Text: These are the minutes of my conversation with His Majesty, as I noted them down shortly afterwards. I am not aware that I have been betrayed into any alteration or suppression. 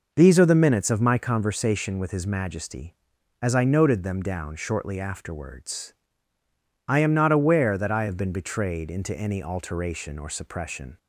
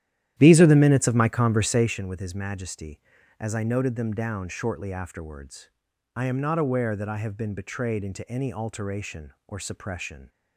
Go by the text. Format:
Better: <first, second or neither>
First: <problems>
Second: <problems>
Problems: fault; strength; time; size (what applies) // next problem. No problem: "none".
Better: first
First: none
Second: starts louder than the rest; strong; until 2.0 s; 12 dB